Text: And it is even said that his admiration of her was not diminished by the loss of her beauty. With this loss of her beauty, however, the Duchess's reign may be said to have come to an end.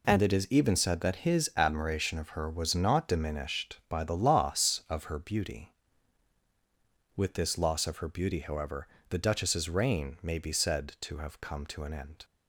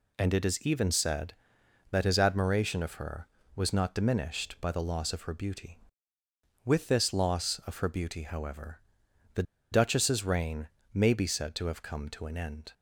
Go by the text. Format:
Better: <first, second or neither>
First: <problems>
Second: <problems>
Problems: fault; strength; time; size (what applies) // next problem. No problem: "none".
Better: first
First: none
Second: pauses between "the" and "Duchess's"; slight; at 9.4 s; 0.28 s long // pauses between "reign" and "may"; slight; at 10.6 s; 0.26 s long